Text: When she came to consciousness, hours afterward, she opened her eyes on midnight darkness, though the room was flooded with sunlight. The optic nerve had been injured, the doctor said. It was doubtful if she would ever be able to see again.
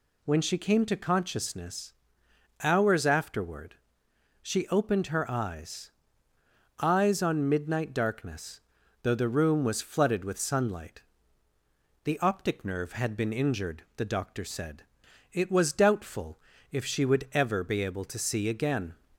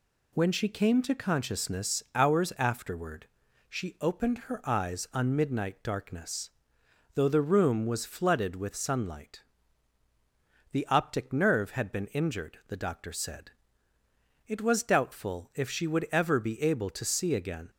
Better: second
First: says "eyes" twice; at 6.8 s // pauses between "doubtful" and "if"; slight; at 16.4 s; 0.32 s long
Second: none

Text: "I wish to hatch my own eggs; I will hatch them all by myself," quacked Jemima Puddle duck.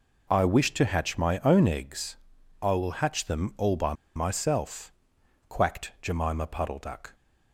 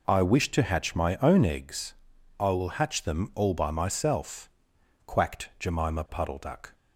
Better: second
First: pauses between "by" and "myself"; slight; at 3.9 s; 0.21 s long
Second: none

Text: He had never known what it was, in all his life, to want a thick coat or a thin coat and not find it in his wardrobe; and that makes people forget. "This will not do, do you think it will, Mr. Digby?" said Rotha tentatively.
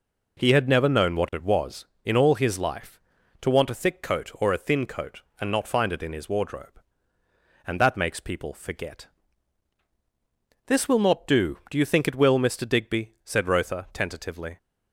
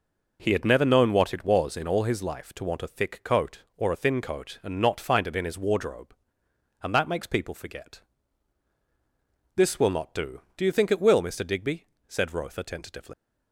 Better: first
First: none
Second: leaves "tentatively" unfinished; at 13.1 s; 120 ms

